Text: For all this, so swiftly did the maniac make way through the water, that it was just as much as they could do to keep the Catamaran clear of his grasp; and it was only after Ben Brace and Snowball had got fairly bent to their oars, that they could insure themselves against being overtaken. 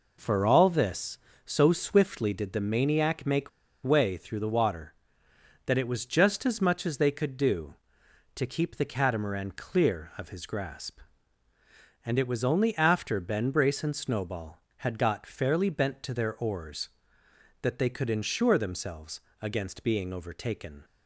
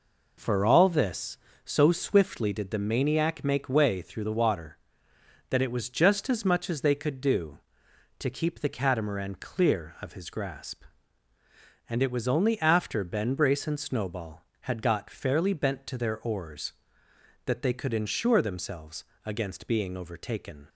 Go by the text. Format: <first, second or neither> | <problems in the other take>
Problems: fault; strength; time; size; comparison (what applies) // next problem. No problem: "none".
second | pauses between "make" and "way"; slight; at 3.4 s; 0.33 s long // pauses between "themselves" and "against"; slight; at 19.2 s; 0.20 s long; slight in the second